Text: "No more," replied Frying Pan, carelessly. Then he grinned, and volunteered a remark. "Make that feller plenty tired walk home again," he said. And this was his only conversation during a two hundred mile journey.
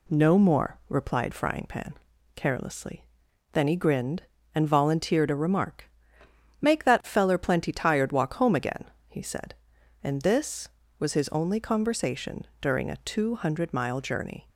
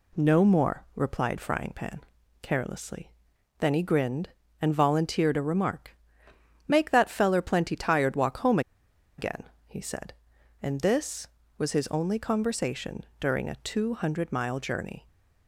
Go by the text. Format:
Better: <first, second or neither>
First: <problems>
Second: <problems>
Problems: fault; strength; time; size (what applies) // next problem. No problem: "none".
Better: first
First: pauses between "conversation" and "during"; slight; at 12.4 s; 0.16 s long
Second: pauses between "home" and "again"; noticeable; at 8.5 s; 0.58 s long // pauses between "conversation" and "during"; slight; at 13.0 s; 0.16 s long